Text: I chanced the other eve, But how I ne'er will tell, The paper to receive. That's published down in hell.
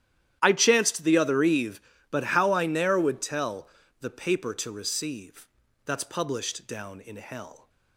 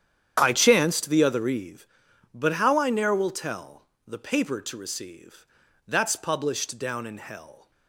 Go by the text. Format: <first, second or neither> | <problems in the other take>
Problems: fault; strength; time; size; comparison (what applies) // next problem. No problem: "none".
second | starts louder than the rest; strong; until 1.4 s; 11.5 dB; strong in the second // says "would" for "will"; at 2.9 s